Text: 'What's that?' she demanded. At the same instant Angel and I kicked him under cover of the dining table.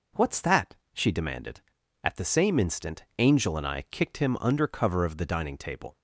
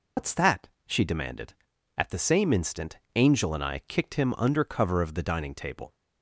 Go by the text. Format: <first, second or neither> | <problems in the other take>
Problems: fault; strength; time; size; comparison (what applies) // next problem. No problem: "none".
first | loses the start of "What's"; at 0.1 s; 110 ms // pauses between "instant" and "Angel"; slight; at 2.9 s; 0.17 s long